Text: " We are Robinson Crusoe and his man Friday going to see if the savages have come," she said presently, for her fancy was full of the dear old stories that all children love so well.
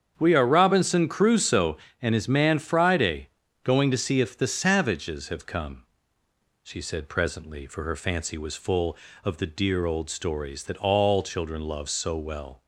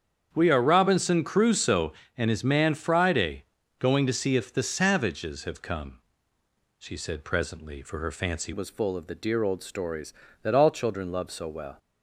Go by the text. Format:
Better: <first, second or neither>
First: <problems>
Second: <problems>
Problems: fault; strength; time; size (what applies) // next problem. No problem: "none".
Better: first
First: starts louder than the rest; strong; until 1.1 s; 8 dB // pauses between "Friday" and "going"; slight; at 3.2 s; 0.36 s long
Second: starts louder than the rest; strong; until 1.3 s; 8 dB // pauses between "Friday" and "going"; slight; at 3.4 s; 0.36 s long // changes voice at "was"; from 8.5 s on; 3.2 s long